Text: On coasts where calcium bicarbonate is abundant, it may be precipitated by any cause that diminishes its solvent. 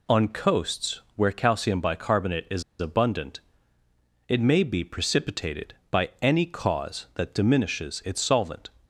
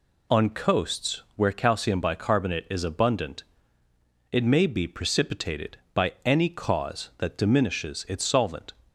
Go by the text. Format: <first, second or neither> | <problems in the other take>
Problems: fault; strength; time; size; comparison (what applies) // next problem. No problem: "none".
second | pauses between "coasts" and "where"; slight; at 0.9 s; 0.16 s long // pauses between "is" and "abundant"; slight; at 2.6 s; 0.18 s long